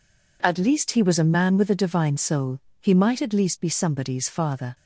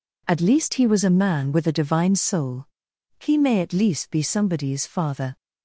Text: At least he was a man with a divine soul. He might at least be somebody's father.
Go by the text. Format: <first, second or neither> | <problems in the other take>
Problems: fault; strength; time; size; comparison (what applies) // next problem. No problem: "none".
first | says "may" for "might"; at 3.3 s